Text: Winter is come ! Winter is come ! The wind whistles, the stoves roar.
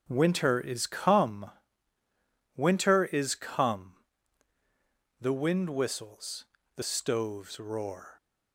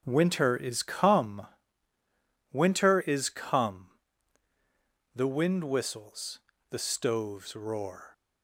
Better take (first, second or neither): neither